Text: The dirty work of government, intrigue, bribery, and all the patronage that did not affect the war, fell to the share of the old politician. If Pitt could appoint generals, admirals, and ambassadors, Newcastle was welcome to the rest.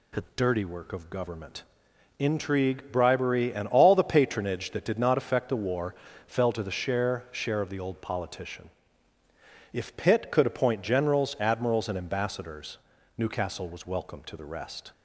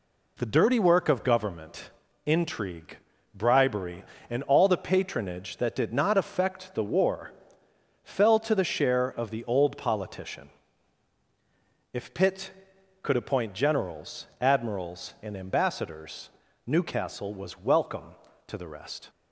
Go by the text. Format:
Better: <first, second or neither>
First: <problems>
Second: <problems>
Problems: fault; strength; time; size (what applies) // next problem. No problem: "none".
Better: second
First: says "share" twice; at 7.3 s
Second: none